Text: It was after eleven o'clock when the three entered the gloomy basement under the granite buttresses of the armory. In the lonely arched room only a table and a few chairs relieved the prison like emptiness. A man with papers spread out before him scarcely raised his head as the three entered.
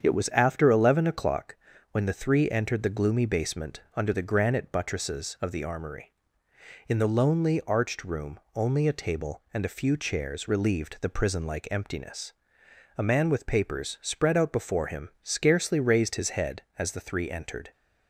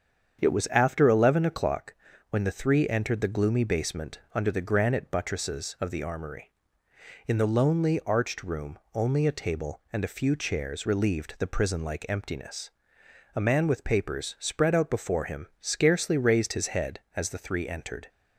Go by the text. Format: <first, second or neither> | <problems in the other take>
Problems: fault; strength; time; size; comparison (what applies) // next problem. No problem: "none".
neither | starts louder than the rest; strong; the same in both // pauses between "o'clock" and "when"; slight; the same in both // pauses between "room" and "only"; slight; the same in both